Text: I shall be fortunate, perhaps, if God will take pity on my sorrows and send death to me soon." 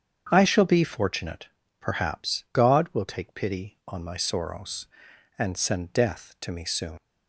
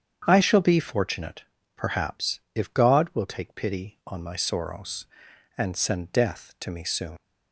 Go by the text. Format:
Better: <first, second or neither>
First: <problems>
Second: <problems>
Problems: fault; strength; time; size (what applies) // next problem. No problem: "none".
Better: second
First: starts louder than the rest; strong; until 1.3 s; 8 dB // skips "if"; at 2.4 s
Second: starts louder than the rest; strong; until 1.2 s; 8 dB